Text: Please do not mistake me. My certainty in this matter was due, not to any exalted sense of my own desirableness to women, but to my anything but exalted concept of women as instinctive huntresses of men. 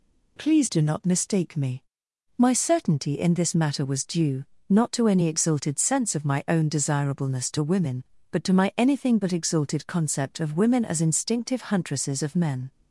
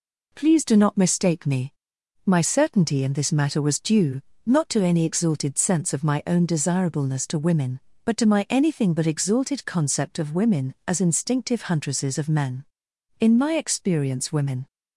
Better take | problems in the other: first | goes on to say "In my experience women"; from 13.1 s on; 1.4 s long

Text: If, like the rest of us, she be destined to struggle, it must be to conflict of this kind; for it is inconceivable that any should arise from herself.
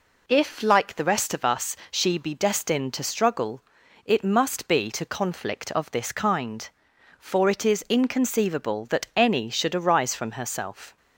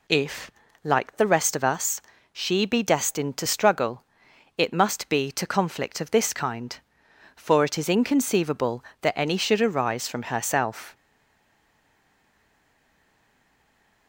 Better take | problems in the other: first | stays silent after the last word; strong; from 10.9 s on; 3.1 s long

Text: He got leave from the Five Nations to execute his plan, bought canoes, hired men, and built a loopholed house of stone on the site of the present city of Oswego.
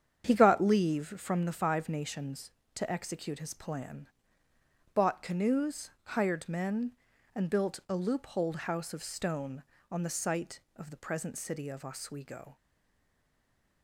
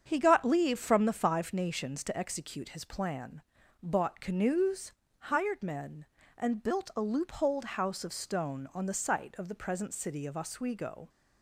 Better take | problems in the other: second | starts louder than the rest; strong; until 1.4 s; 8 dB; strong in the second // stays silent after the last word; noticeable; from 12.5 s on; 1.3 s long

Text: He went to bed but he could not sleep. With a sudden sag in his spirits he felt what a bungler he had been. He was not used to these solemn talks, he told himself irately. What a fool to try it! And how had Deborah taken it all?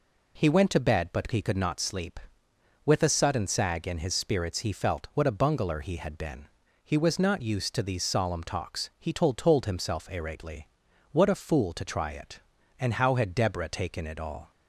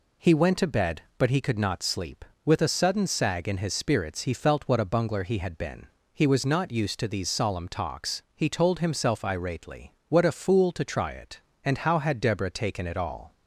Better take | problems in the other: second | says "told" twice; at 9.3 s

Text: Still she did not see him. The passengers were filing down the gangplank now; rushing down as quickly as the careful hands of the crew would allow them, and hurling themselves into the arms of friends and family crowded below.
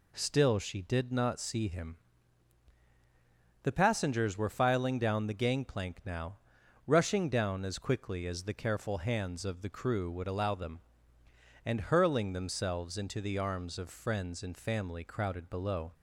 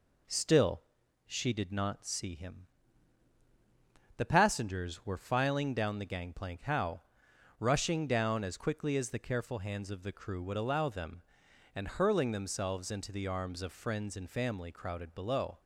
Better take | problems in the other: first | pauses between "Still" and "she"; at 0.8 s; 0.44 s long // says "how" for "now"; at 6.6 s

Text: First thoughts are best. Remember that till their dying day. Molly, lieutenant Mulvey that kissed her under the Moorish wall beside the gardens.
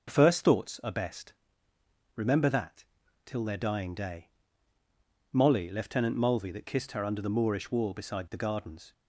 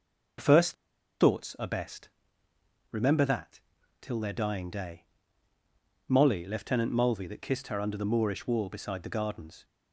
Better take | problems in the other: first | pauses between "First" and "thoughts"; noticeable; at 0.7 s; 0.47 s long // pauses between "that" and "till"; at 3.5 s; 0.44 s long; also in the first

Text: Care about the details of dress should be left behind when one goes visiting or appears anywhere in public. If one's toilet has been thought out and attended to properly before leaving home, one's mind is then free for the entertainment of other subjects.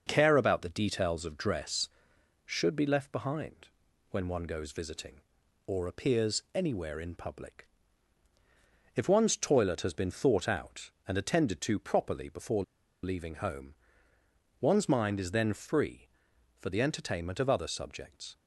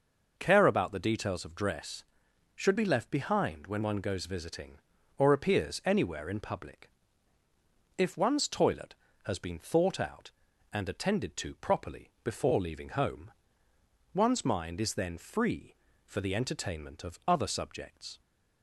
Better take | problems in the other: second | starts louder than the rest; noticeable; until 1.0 s; 6 dB // pauses between "behind" and "when"; at 3.6 s; 0.42 s long // pauses between "before" and "leaving"; at 12.6 s; 0.39 s long

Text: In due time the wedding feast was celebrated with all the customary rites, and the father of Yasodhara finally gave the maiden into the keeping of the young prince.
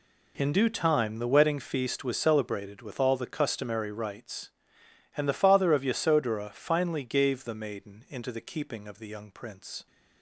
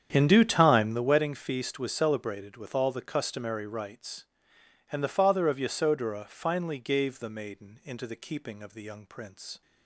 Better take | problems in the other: first | starts louder than the rest; strong; until 1.1 s; 8.5 dB

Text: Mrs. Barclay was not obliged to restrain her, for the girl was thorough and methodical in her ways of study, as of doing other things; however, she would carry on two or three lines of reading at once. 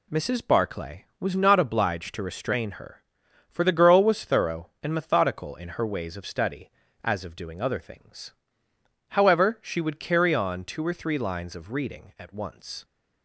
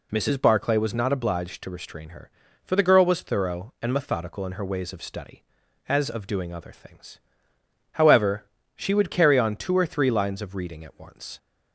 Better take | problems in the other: neither | none

